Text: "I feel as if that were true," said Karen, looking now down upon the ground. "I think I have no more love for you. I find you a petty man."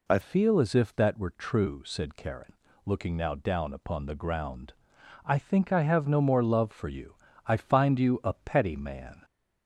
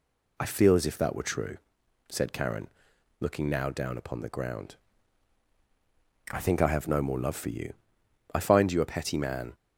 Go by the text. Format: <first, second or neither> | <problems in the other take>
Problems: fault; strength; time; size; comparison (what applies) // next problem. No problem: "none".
second | changes voice at "feel"; from 0.2 s on; 9.0 s long